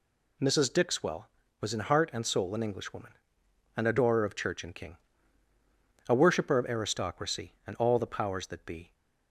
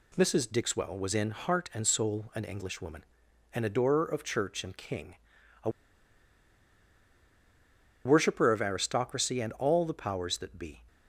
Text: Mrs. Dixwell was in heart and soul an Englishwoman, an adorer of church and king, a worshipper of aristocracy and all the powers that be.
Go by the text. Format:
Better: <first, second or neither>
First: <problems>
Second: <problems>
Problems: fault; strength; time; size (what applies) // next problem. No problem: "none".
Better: first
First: none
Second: pauses between "a" and "worshipper"; strong; at 5.7 s; 2.3 s long